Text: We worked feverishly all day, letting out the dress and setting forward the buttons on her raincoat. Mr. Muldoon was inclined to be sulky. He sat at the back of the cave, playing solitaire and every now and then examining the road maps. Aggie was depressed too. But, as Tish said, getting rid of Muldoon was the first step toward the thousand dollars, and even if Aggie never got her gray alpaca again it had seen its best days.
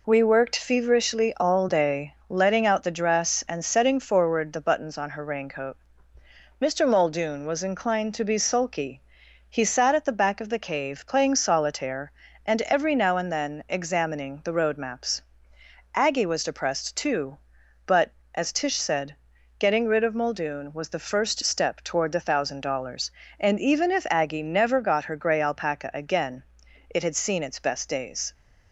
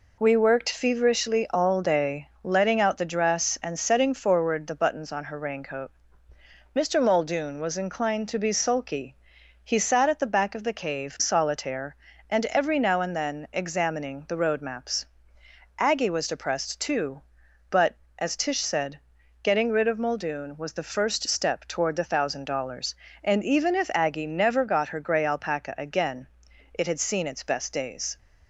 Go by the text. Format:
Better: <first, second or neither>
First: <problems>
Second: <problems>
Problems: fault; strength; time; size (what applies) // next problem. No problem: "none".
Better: first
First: pauses between "again" and "it"; at 26.4 s; 0.44 s long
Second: skips "playing"; at 11.1 s // pauses between "again" and "it"; at 26.2 s; 0.44 s long